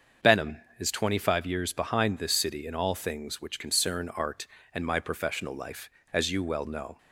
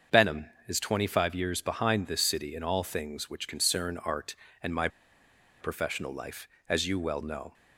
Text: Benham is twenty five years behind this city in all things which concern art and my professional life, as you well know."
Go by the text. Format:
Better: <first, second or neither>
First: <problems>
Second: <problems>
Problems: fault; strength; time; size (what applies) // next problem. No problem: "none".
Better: first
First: starts louder than the rest; until 1.4 s; 7 dB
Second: starts louder than the rest; until 1.3 s; 7 dB // pauses between "my" and "professional"; noticeable; at 4.8 s; 0.72 s long